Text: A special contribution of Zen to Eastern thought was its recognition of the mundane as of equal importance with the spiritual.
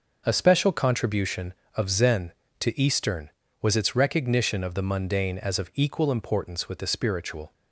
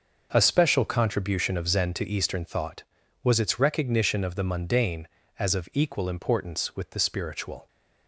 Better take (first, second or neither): second